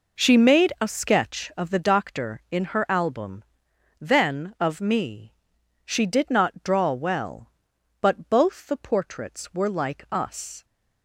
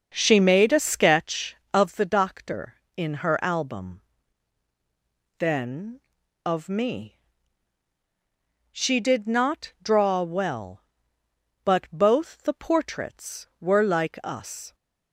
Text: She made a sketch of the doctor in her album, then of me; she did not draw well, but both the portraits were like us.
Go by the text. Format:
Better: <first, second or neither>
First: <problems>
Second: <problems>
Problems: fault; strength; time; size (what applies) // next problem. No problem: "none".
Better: first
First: none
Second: starts louder than the rest; until 1.3 s; 6 dB